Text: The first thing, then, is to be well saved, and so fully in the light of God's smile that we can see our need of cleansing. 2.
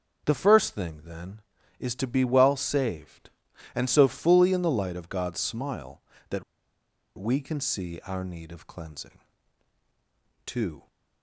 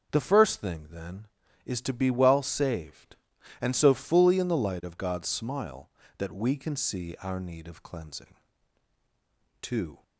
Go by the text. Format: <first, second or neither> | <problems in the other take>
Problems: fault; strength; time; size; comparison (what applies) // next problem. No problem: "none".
second | starts louder than the rest; until 1.2 s; 6.5 dB; also in the second // pauses between "that" and "we"; noticeable; at 6.4 s; 0.75 s long